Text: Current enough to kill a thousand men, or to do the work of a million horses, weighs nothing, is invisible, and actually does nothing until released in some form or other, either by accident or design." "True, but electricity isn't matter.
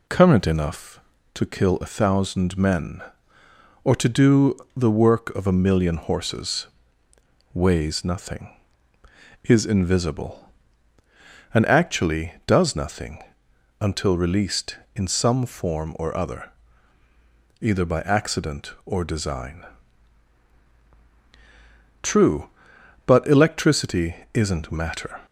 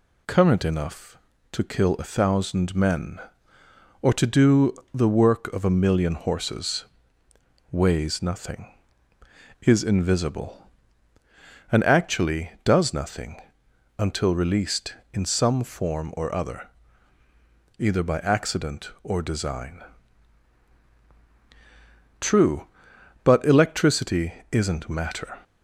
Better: second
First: starts louder than the rest; slight; until 1.3 s; 2.5 dB // pauses between "do" and "the"; slight; at 4.5 s; 0.20 s long // pauses between "nothing" and "until"; noticeable; at 13.2 s; 0.60 s long // pauses between "electricity" and "isn't"; slight; at 24.1 s; 0.18 s long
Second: pauses between "do" and "the"; slight; at 4.7 s; 0.20 s long // pauses between "nothing" and "until"; noticeable; at 13.3 s; 0.60 s long // pauses between "electricity" and "isn't"; slight; at 24.3 s; 0.18 s long

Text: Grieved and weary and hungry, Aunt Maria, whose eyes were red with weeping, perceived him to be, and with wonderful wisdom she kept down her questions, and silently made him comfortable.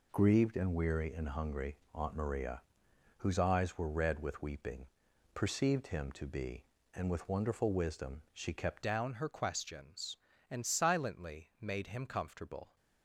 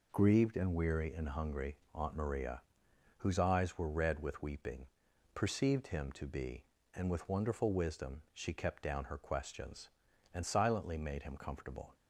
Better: second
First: changes voice at "down"; from 8.8 s on; 3.9 s long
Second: none

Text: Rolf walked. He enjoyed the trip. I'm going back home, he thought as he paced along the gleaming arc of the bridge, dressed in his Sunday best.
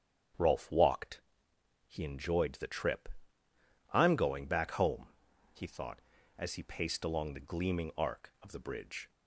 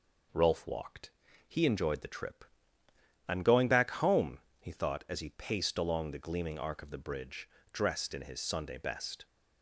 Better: second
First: starts louder than the rest; strong; until 2.0 s; 9 dB // stops before "dressed in his Sunday best"; at 9.0 s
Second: none

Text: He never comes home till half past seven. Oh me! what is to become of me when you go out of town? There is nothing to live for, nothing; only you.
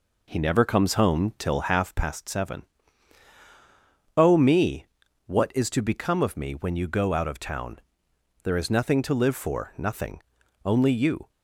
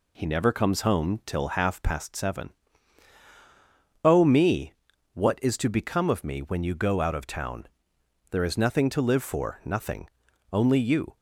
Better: second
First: starts louder than the rest; until 1.9 s; 4 dB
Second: none

